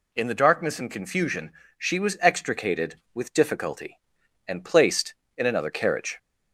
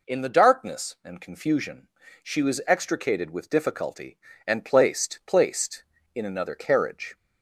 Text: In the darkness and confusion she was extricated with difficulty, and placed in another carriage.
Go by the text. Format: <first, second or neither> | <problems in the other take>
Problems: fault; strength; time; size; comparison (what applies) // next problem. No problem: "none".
first | pauses between "confusion" and "she"; slight; at 1.8 s; 0.34 s long; slight in the first // says "placed" twice; at 5.2 s